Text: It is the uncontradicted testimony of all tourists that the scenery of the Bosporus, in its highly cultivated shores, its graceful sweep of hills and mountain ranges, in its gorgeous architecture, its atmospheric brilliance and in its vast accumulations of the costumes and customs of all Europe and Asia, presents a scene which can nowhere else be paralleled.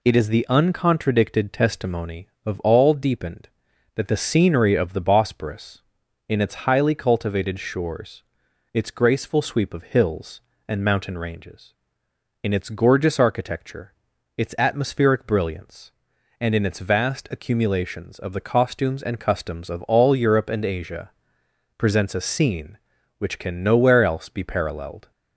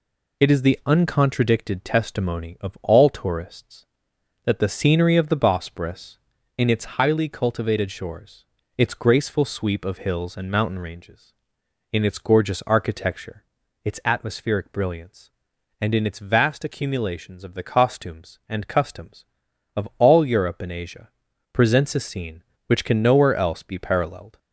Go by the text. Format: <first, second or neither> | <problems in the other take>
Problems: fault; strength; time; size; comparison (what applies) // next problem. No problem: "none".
second | says "deepened" for "tourists"; at 2.9 s